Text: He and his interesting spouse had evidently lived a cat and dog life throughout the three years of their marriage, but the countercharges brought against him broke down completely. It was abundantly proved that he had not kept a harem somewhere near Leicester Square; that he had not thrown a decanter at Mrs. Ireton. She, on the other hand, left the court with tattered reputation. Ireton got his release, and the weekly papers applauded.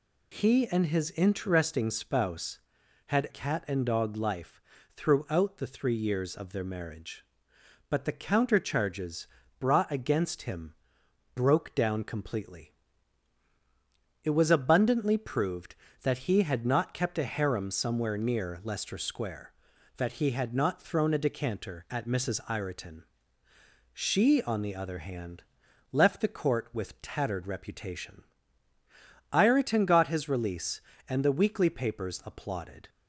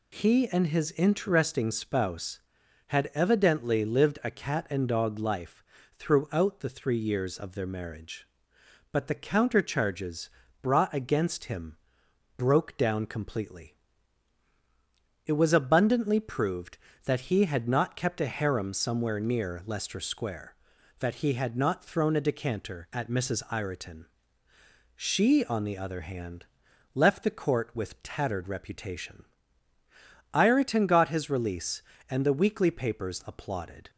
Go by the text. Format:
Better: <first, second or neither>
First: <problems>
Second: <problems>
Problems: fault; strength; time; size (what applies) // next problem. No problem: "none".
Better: second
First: skips "evidently lived a"; at 3.2 s // pauses between "life" and "throughout"; slight; at 4.6 s; 0.34 s long // pauses between "countercharges" and "brought"; slight; at 9.2 s; 0.32 s long // pauses between "him" and "broke"; noticeable; at 10.7 s; 0.60 s long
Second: pauses between "life" and "throughout"; slight; at 5.6 s; 0.34 s long // pauses between "countercharges" and "brought"; slight; at 10.2 s; 0.32 s long // pauses between "him" and "broke"; noticeable; at 11.7 s; 0.60 s long